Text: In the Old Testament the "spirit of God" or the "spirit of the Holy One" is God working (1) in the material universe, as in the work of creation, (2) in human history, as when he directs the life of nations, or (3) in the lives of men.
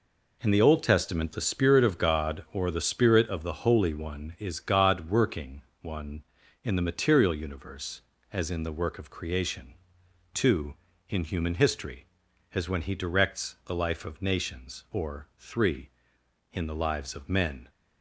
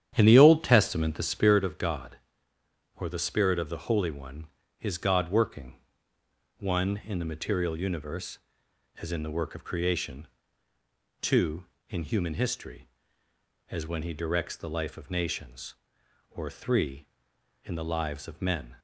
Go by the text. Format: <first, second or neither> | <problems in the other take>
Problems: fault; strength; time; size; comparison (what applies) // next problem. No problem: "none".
first | starts louder than the rest; strong; until 1.5 s; 9.5 dB